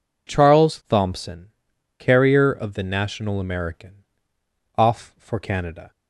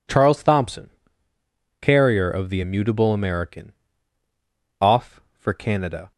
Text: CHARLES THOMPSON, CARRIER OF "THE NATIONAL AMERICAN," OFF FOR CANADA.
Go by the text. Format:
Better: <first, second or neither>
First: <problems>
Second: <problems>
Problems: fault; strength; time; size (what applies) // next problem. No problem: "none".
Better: first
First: none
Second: says "Immutable" for "NATIONAL"; at 2.6 s